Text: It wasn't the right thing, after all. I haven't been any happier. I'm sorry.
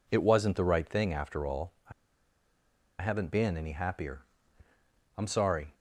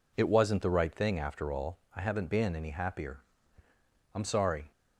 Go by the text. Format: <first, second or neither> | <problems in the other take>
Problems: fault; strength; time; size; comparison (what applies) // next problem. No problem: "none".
second | pauses between "I" and "haven't"; at 1.9 s; 1.0 s long